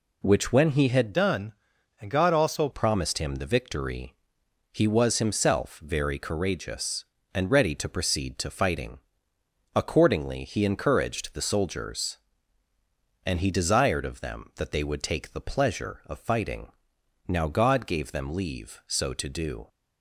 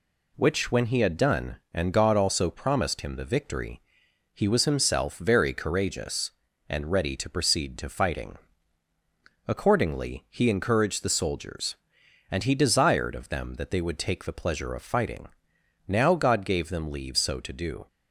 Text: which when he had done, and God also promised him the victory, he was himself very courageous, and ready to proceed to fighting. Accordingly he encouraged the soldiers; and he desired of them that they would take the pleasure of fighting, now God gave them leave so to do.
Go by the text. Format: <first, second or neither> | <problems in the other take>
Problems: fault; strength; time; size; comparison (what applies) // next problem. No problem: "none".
second | changes voice from "done" to "also"; from 1.1 to 2.6 s; 1.5 s long